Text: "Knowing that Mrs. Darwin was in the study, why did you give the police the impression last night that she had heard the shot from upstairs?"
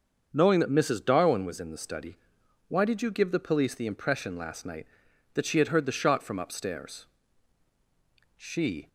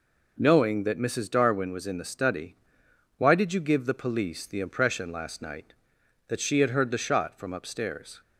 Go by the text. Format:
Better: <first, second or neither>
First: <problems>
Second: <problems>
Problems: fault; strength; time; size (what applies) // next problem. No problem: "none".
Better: second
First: starts louder than the rest; until 1.3 s; 6.5 dB // goes on to say "She"; from 8.3 s on; 0.50 s long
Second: none